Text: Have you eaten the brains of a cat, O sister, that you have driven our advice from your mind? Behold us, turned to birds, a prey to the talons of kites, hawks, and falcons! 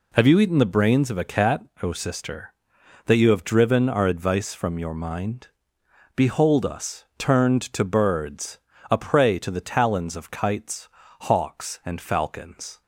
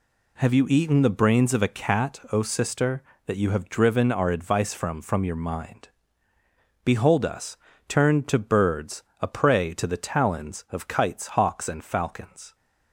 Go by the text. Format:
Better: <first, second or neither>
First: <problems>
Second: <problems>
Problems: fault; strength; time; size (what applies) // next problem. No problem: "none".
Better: first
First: none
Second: says "from" twice; at 4.9 s